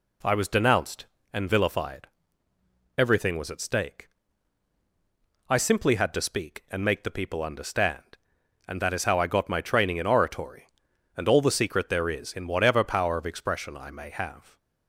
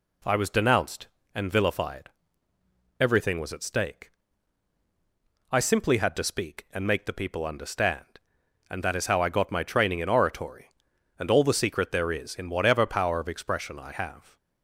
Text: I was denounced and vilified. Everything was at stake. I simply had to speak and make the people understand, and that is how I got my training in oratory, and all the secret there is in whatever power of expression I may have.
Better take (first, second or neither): first